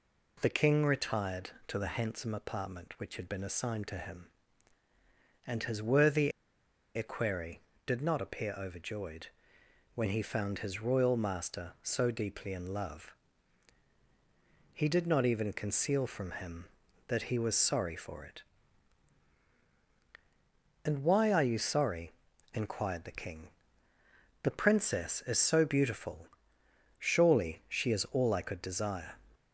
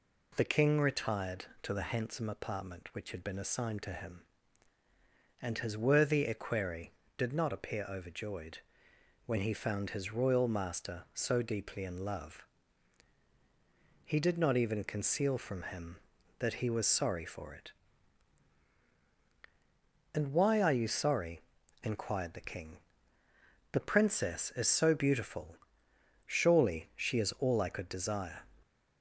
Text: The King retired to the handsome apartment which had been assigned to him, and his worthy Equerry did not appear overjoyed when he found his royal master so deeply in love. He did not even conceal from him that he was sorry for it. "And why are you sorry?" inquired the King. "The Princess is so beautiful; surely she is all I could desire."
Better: second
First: pauses between "worthy" and "Equerry"; noticeable; at 6.3 s; 0.64 s long // pauses between "overjoyed" and "when"; noticeable; at 9.2 s; 0.70 s long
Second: pauses between "overjoyed" and "when"; noticeable; at 8.5 s; 0.70 s long

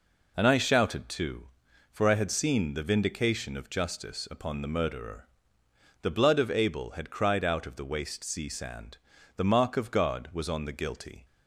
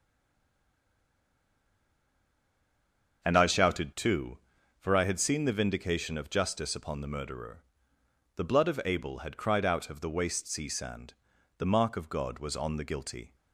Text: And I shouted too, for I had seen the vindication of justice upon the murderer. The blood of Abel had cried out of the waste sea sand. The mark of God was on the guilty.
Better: first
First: none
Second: stays silent before the first word; strong; until 3.2 s; 3.2 s long // starts louder than the rest; until 4.2 s; 6.5 dB

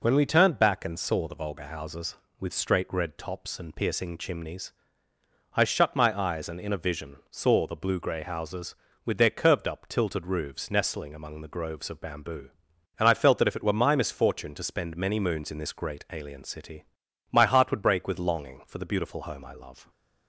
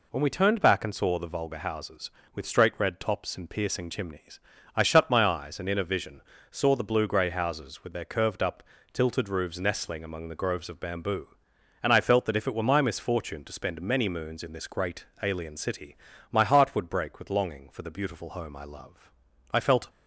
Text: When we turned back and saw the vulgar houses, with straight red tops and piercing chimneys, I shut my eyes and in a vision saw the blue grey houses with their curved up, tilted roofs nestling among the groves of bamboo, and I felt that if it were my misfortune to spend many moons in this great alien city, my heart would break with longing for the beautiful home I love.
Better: first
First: none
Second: pauses between "vision" and "saw"; slight; at 6.2 s; 0.30 s long // pauses between "great" and "alien"; slight; at 15.0 s; 0.18 s long // goes on to say "I felt"; slight; from 19.5 s on; 0.38 s long

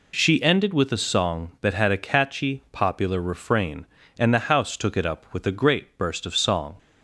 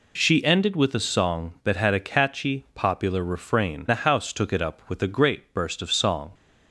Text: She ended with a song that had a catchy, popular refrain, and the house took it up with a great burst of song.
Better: first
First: none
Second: skips "and"; at 3.8 s

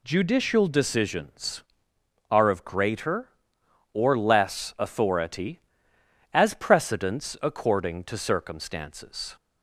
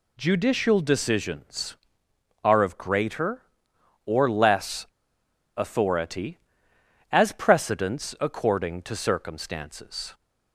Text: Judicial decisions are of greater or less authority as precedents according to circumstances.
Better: first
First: none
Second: pauses between "less" and "authority"; noticeable; at 4.8 s; 0.71 s long

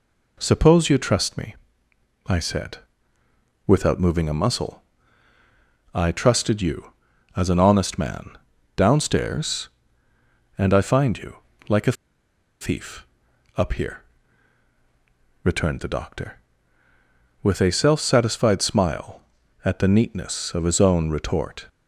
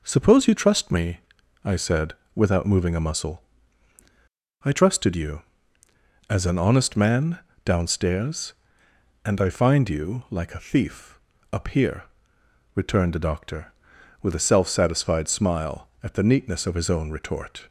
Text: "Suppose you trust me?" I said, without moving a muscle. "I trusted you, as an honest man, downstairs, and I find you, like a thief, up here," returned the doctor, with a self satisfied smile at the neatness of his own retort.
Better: second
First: pauses between "a" and "thief"; noticeable; at 11.9 s; 0.68 s long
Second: none

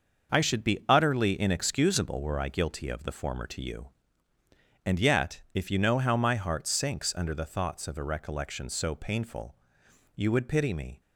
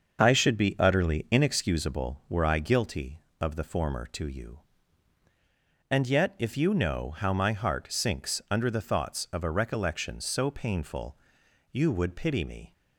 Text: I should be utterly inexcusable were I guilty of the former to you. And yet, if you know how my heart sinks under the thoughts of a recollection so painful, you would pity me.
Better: neither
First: starts louder than the rest; until 1.4 s; 6.5 dB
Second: starts louder than the rest; until 1.2 s; 6 dB

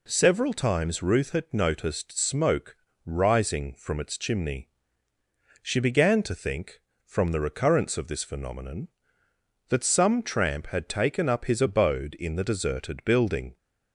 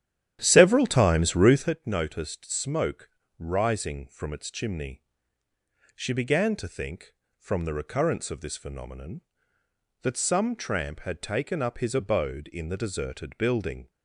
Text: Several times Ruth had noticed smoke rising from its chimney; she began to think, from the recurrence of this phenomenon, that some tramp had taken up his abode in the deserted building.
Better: first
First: pauses between "smoke" and "rising"; slight; at 2.7 s; 0.28 s long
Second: starts louder than the rest; strong; until 1.8 s; 11 dB // pauses between "smoke" and "rising"; slight; at 3.0 s; 0.28 s long

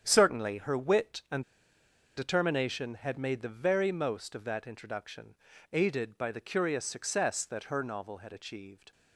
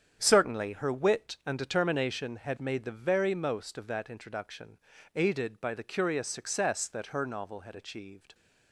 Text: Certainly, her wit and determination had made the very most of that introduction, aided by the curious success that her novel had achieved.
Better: second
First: starts louder than the rest; strong; until 1.0 s; 8.5 dB // pauses between "and" and "determination"; noticeable; at 1.4 s; 0.74 s long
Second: starts louder than the rest; strong; until 1.2 s; 8.5 dB

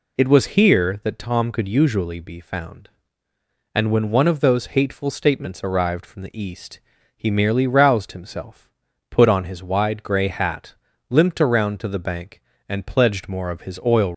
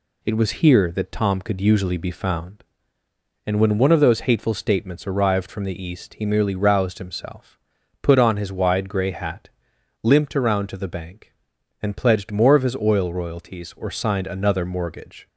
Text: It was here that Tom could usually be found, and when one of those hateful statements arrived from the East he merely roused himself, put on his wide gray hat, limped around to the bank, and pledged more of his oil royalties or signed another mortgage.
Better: second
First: pauses between "East" and "he"; slight; at 6.7 s; 0.36 s long // stops before "royalties or signed another mortgage"; at 14.1 s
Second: none

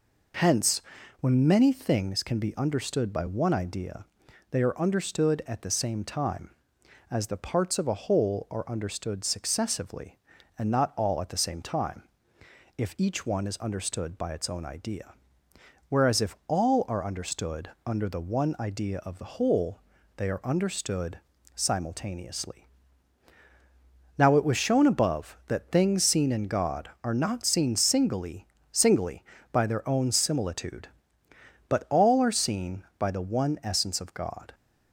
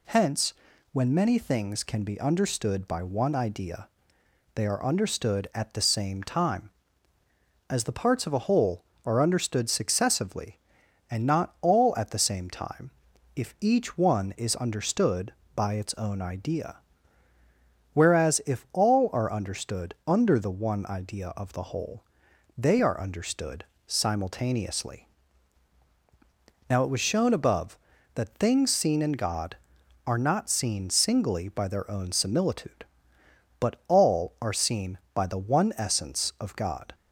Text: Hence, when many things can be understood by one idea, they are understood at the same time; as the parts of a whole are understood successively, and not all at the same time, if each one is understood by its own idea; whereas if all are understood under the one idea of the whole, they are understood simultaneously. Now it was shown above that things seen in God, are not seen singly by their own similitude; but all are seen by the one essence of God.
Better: second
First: pauses between "understood" and "under"; slight; at 17.6 s; 0.16 s long // pauses between "understood" and "simultaneously"; slight; at 21.1 s; 0.34 s long // says "singly" twice; at 28.7 s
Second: pauses between "understood" and "simultaneously"; slight; at 23.6 s; 0.22 s long

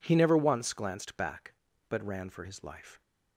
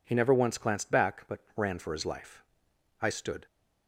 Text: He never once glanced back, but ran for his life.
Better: first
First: none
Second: pauses between "but" and "ran"; slight; at 1.3 s; 0.16 s long // goes on to say "I stood"; slight; from 3.0 s on; 0.44 s long

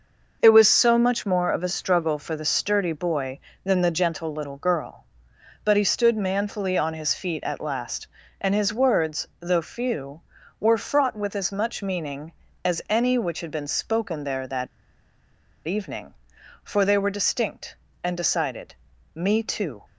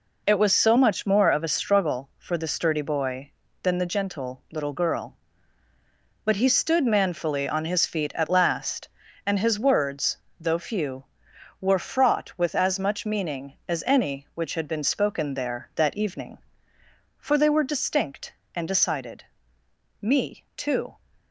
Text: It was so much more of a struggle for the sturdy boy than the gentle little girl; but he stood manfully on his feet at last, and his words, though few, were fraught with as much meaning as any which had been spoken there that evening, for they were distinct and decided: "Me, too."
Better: second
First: pauses between "that" and "evening"; at 14.6 s; 1.0 s long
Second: none

